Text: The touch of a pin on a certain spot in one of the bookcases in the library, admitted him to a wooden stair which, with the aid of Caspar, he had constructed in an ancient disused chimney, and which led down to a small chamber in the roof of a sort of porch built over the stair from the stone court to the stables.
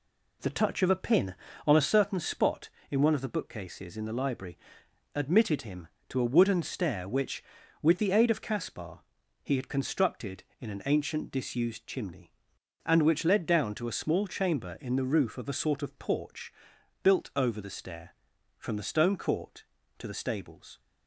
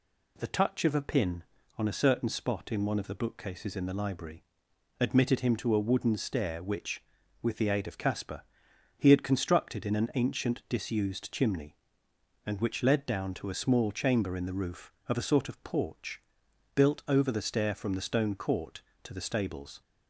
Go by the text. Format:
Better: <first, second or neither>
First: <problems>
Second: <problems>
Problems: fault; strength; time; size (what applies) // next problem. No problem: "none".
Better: second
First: starts louder than the rest; slight; until 2.0 s; 2.5 dB // pauses between "porch" and "built"; noticeable; at 16.5 s; 0.52 s long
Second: pauses between "porch" and "built"; noticeable; at 16.2 s; 0.54 s long